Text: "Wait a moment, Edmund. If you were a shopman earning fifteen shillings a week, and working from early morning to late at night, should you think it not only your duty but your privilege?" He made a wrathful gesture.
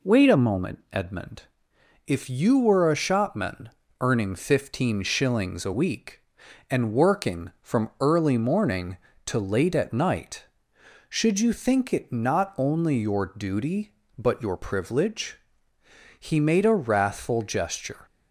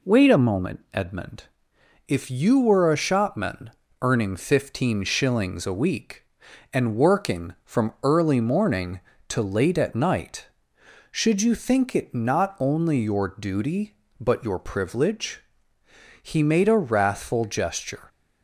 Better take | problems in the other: neither | pauses between "shopman" and "earning"; slight; the same in both

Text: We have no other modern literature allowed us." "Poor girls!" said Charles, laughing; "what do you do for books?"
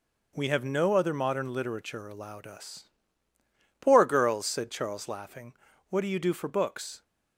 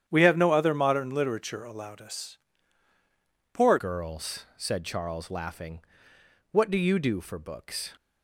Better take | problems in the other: first | starts louder than the rest; strong; until 1.0 s; 9.5 dB // changes voice at "girls"; from 3.7 s on; 4.2 s long

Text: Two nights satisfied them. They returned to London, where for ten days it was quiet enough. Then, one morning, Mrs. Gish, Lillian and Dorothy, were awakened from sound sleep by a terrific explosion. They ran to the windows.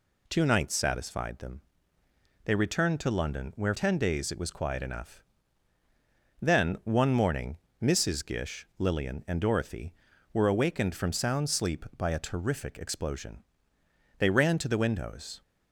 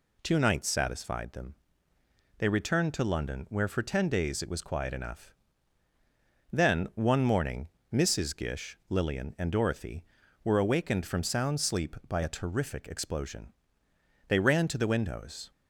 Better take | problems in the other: second | skips "for"; at 3.7 s

